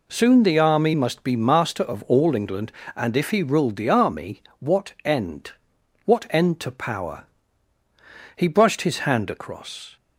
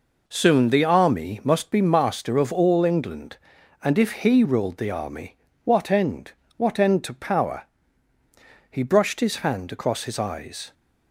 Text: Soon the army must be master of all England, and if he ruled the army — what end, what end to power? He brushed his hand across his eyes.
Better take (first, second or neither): second